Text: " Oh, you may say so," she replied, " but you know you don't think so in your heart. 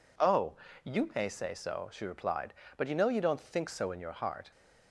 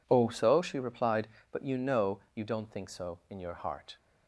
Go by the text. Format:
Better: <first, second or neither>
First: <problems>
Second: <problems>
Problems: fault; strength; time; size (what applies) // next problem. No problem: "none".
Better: first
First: none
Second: skips "you may say"; at 0.2 s